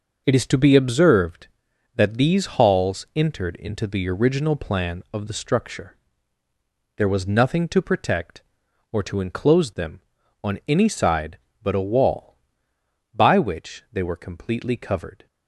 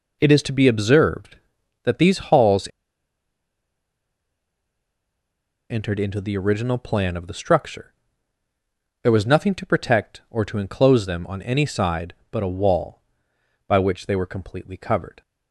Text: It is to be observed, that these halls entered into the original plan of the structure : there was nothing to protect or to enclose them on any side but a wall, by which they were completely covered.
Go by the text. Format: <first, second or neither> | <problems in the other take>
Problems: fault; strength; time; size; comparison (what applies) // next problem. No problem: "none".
first | pauses between "halls" and "entered"; strong; at 2.6 s; 3.0 s long